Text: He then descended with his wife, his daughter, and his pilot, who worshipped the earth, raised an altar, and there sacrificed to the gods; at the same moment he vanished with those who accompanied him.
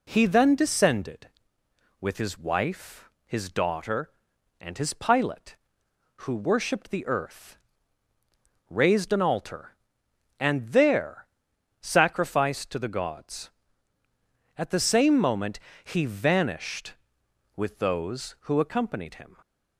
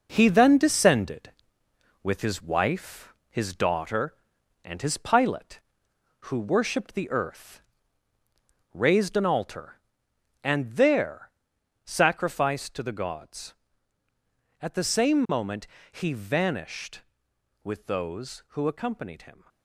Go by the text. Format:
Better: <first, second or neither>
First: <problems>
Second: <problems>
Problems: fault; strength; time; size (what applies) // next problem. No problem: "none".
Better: first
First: pauses between "there" and "sacrificed"; noticeable; at 11.2 s; 0.54 s long // pauses between "moment" and "he"; slight; at 15.5 s; 0.24 s long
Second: gets quieter; throughout; 6.5 dB // pauses between "there" and "sacrificed"; noticeable; at 11.3 s; 0.54 s long // pauses between "moment" and "he"; slight; at 15.6 s; 0.24 s long